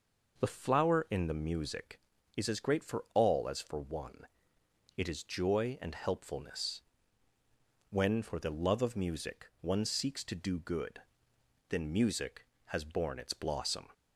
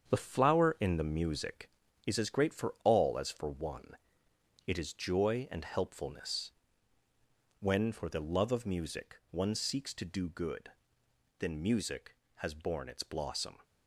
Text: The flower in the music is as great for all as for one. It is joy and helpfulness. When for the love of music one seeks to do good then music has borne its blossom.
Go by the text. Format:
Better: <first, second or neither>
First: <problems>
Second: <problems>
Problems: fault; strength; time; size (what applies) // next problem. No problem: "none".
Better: first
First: pauses between "good" and "then"; noticeable; at 10.9 s; 0.70 s long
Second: gets quieter; strong; throughout; 8 dB // pauses between "good" and "then"; noticeable; at 10.6 s; 0.70 s long